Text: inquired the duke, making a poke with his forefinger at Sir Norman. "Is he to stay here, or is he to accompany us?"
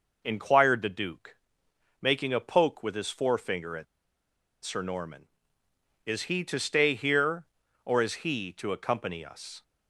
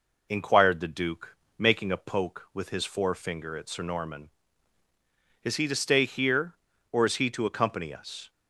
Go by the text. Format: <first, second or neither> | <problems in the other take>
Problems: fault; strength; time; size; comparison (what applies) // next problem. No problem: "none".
second | pauses between "at" and "Sir"; noticeable; at 3.8 s; 0.79 s long